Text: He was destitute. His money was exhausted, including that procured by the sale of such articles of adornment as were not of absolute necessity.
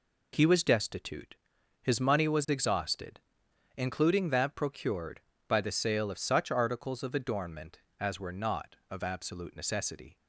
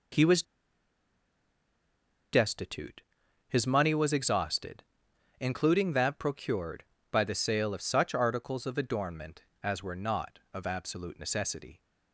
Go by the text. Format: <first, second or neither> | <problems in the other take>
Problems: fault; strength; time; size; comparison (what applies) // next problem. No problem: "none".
first | pauses between "was" and "destitute"; strong; at 0.4 s; 1.8 s long